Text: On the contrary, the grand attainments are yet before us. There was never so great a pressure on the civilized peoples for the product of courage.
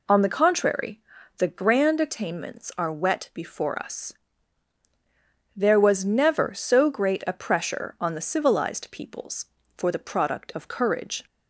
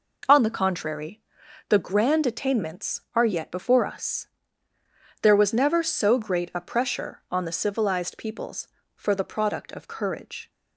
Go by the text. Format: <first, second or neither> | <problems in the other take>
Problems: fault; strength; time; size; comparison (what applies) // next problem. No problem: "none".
second | says "wet" for "yet"; at 2.9 s